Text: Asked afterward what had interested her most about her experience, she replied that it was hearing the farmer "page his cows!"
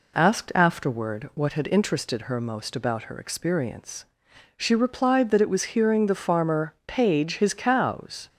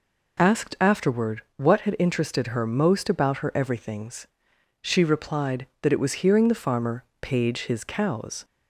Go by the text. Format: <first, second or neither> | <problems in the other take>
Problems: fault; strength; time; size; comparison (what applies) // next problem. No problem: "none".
first | says "everythings" for "experience"; at 3.5 s // pauses between "farmer" and "page"; slight; at 7.0 s; 0.18 s long